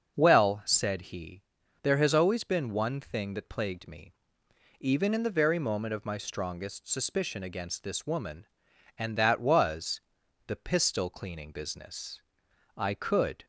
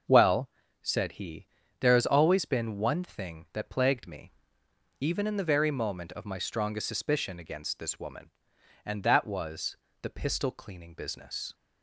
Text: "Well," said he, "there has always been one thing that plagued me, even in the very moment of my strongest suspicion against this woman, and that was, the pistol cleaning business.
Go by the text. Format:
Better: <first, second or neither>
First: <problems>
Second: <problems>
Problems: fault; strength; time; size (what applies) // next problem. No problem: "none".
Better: second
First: starts louder than the rest; until 1.1 s; 6.5 dB // goes on to say "I could"; noticeable; from 12.7 s on; 0.68 s long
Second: starts louder than the rest; until 1.4 s; 6.5 dB